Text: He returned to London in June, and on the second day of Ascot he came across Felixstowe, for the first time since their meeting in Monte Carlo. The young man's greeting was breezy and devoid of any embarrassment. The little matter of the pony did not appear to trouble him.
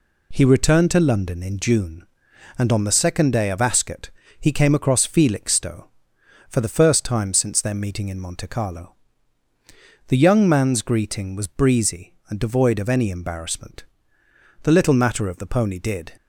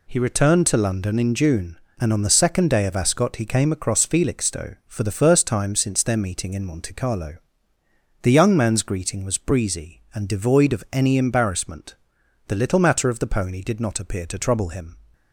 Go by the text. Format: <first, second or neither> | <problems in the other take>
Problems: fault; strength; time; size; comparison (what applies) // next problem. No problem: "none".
second | pauses between "Ascot" and "he"; slight; at 4.0 s; 0.30 s long // stops before "not appear to trouble him"; at 16.1 s